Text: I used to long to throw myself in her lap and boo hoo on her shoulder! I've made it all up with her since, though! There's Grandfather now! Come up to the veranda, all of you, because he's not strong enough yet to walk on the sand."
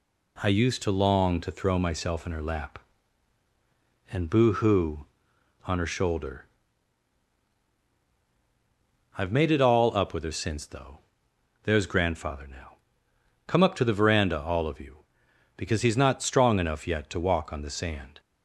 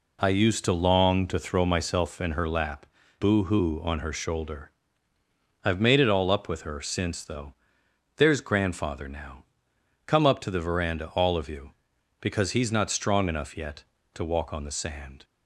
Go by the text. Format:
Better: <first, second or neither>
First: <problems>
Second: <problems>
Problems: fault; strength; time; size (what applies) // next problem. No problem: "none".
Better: first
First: none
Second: skips "and"; at 3.0 s